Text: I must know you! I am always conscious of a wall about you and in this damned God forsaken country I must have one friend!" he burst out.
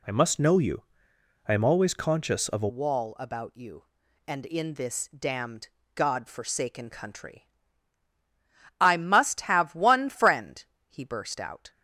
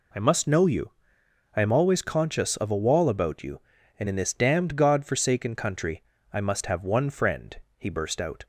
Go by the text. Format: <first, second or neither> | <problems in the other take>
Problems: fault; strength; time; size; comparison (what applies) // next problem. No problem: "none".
second | changes voice at "wall"; from 2.6 s on; 9.0 s long // pauses between "damned" and "God"; slight; at 5.6 s; 0.26 s long // pauses between "country" and "I"; strong; at 7.4 s; 1.3 s long; slight in the second